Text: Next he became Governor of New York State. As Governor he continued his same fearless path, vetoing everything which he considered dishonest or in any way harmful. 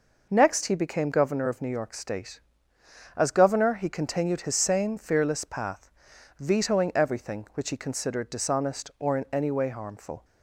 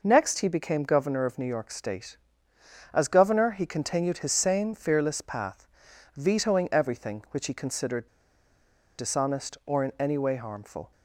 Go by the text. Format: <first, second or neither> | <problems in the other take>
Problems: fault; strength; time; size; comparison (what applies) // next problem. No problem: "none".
first | pauses between "considered" and "dishonest"; noticeable; at 8.0 s; 0.91 s long